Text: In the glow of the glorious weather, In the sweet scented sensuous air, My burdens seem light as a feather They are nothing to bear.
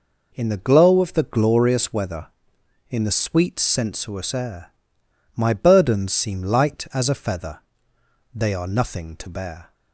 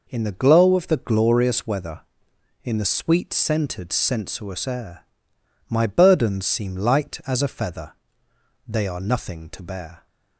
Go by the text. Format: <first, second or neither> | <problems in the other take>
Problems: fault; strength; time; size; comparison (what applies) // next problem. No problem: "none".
second | skips "scented"; at 3.5 s // pauses between "feather" and "They"; noticeable; at 7.5 s; 0.76 s long; noticeable in the second